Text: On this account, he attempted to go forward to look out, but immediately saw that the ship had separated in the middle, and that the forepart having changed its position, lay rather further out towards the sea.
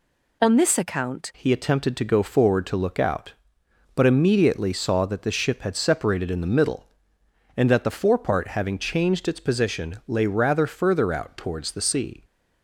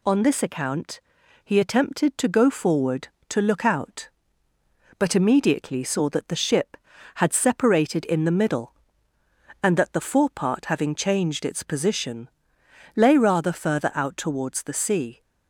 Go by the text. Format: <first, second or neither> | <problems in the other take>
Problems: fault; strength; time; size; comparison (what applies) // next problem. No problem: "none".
second | changes voice at "he"; from 1.3 s on; 10.9 s long